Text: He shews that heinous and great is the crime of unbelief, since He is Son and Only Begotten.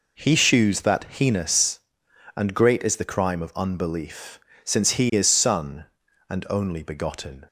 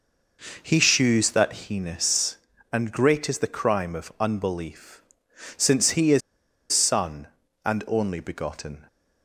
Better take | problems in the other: first | pauses between "is" and "Son"; noticeable; at 6.2 s; 0.52 s long

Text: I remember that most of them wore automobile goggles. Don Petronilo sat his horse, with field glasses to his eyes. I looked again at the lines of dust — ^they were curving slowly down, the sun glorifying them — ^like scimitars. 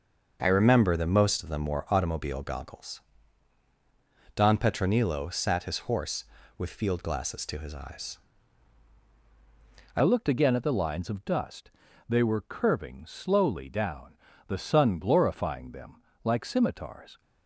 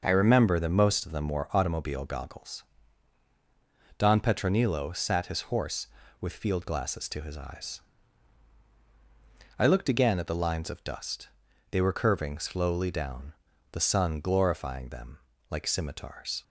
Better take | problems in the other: second | starts louder than the rest; noticeable; until 1.4 s; 6 dB // changes voice at "looked"; from 10.0 s on; 7.2 s long

